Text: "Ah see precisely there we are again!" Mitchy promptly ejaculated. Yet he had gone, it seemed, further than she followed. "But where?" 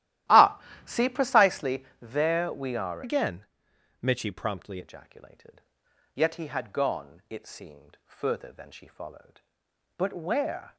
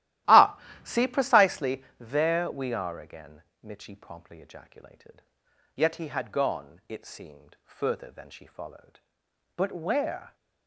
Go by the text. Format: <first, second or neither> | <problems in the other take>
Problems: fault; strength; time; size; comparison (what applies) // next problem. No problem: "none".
second | starts louder than the rest; strong; until 1.5 s; 14 dB; strong in the second // pauses between "Ah" and "see"; slight; at 0.5 s; 0.26 s long; slight in the second // pauses between "precisely" and "there"; slight; at 1.8 s; 0.16 s long; slight in the second // changes voice from "again" to "promptly"; from 3.0 to 4.8 s; 1.8 s long